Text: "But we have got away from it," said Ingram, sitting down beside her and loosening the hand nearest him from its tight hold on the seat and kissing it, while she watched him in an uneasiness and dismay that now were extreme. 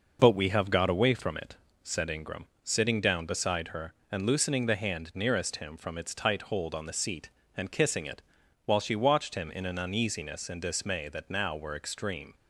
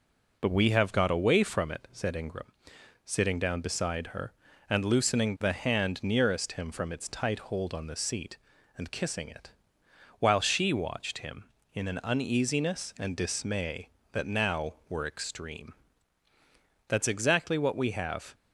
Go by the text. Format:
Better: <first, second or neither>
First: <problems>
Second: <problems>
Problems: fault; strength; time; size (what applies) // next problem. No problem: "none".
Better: first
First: none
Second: goes on to say "That's exactly what we have"; from 16.8 s on; 1.4 s long